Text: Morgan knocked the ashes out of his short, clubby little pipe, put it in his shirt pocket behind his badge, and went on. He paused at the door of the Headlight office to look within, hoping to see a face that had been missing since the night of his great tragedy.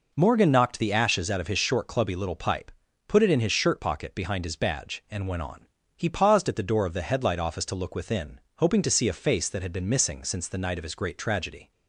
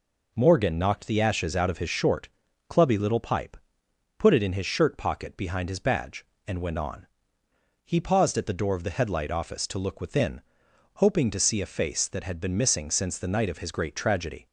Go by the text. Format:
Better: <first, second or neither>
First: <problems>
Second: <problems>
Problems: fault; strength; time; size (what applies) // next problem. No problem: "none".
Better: neither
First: none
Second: none